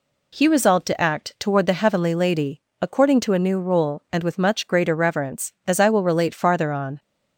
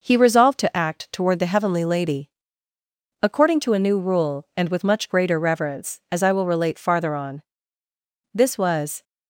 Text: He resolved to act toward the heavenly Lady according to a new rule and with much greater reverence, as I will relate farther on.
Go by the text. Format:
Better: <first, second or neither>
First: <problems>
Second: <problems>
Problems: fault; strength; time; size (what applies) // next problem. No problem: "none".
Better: first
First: pauses between "Lady" and "according"; slight; at 2.5 s; 0.22 s long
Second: pauses between "Lady" and "according"; noticeable; at 2.2 s; 0.96 s long // goes on to say "This was"; noticeable; from 8.3 s on; 0.70 s long